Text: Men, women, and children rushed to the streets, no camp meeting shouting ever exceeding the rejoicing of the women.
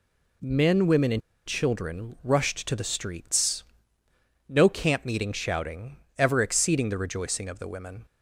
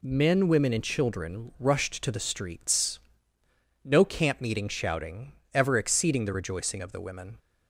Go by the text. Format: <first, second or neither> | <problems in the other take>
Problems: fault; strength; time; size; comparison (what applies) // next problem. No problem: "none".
second | pauses between "and" and "children"; slight; at 1.2 s; 0.26 s long // pauses between "shouting" and "ever"; slight; at 5.9 s; 0.20 s long; slight in the second